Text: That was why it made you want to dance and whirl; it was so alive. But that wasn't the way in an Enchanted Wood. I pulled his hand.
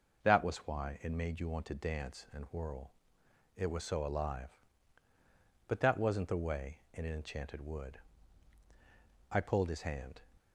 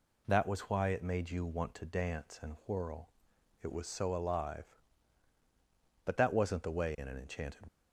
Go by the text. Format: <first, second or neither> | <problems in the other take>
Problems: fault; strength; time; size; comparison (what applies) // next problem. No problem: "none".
first | stops before "Wood I pulled his hand"; at 7.6 s